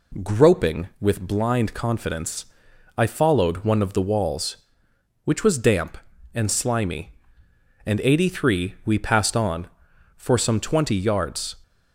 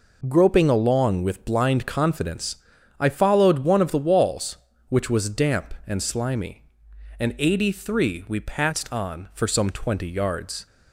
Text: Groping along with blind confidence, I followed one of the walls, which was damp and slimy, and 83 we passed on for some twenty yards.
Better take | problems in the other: second | skips "along"; at 0.9 s

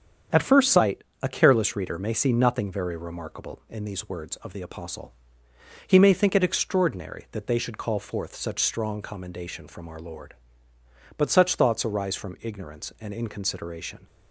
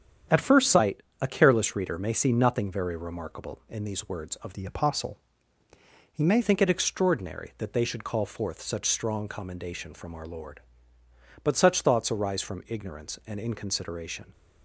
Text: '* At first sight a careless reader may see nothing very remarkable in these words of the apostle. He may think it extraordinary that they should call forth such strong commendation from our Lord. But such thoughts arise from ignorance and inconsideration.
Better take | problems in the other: first | starts louder than the rest; strong; until 1.4 s; 8.5 dB; strong in the first // pauses between "sight" and "a"; slight; at 1.0 s; 0.20 s long; slight in the first // changes voice from "the" to "may"; from 4.5 to 6.4 s; 1.9 s long

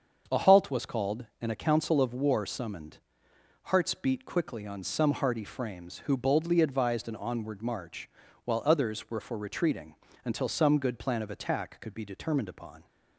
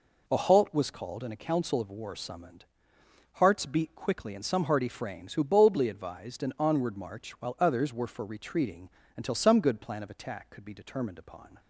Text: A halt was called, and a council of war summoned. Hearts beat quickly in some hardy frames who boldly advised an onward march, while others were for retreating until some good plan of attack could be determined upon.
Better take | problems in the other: second | starts louder than the rest; until 1.4 s; 7 dB // says "on" for "in"; at 4.6 s // pauses between "retreating" and "until"; slight; at 9.9 s; 0.30 s long; slight in the second

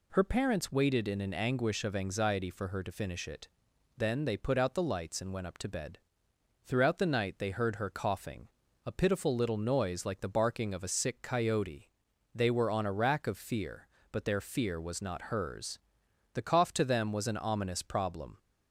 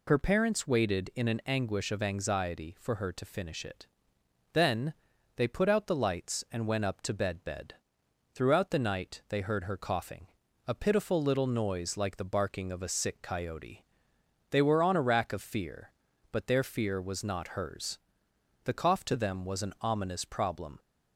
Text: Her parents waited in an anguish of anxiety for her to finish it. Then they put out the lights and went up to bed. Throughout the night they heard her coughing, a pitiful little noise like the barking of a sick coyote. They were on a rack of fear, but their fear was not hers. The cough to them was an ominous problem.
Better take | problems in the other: first | pauses between "Then" and "they"; at 4.9 s; 0.42 s long // says "bed" twice; at 7.4 s

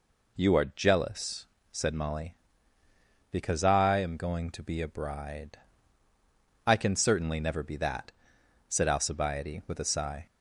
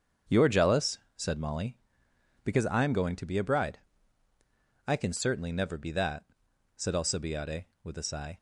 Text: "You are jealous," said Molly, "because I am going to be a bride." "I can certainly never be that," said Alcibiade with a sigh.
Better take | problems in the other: first | gets quieter; strong; throughout; 9 dB

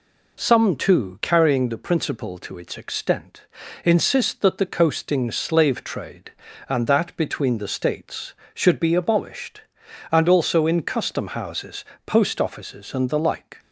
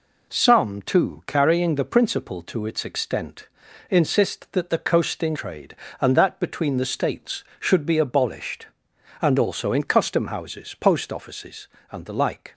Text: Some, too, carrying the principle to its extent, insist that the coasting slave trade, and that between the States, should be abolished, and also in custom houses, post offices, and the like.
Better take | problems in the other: first | skips "slave"; at 5.3 s

